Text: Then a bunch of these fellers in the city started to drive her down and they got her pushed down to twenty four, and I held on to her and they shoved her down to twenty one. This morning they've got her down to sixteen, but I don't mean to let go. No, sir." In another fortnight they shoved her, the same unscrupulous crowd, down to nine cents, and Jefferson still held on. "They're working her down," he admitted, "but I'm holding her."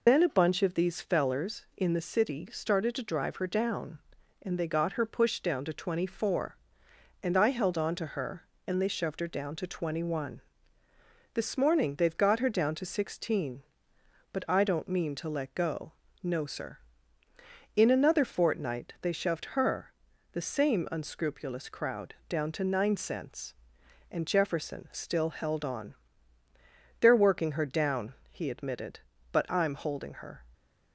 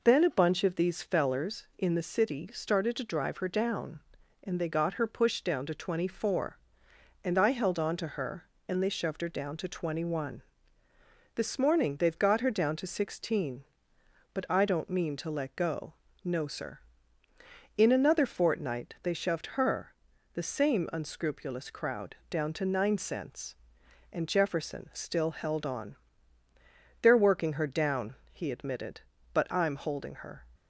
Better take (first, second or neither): second